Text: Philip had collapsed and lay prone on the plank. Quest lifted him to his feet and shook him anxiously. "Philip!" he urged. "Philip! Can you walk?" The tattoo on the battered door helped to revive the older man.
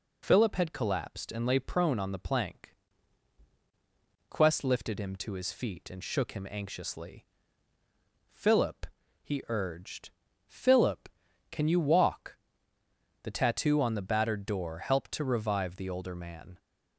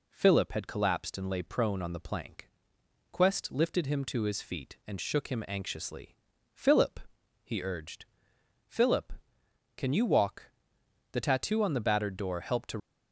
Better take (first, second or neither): first